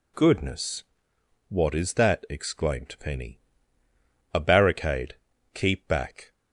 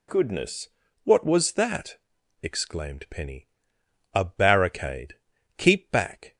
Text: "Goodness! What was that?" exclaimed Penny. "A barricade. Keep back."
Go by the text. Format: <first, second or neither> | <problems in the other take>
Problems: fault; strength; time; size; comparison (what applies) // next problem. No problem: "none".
second | says "is" for "was"; at 1.7 s